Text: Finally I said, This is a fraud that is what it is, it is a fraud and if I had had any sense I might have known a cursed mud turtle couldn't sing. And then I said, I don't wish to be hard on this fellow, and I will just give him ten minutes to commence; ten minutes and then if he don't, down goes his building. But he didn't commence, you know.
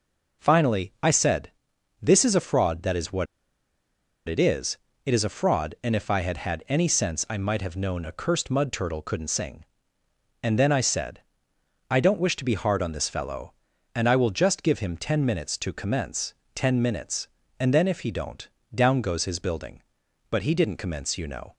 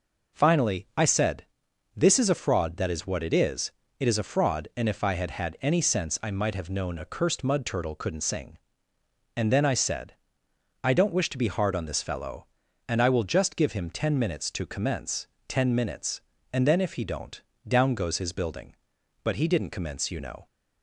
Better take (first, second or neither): second